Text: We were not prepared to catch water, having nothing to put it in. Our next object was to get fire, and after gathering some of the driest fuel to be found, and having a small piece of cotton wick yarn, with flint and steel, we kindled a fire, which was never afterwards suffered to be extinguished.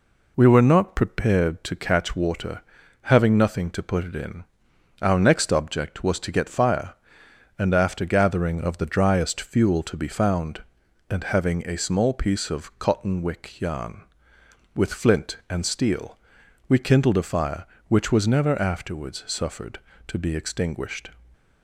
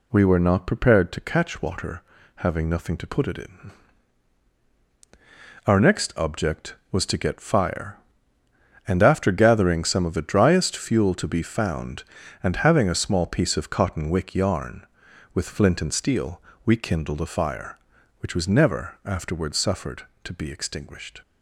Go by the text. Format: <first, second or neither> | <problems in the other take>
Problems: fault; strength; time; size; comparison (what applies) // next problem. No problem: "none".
second | skips "some"; at 8.6 s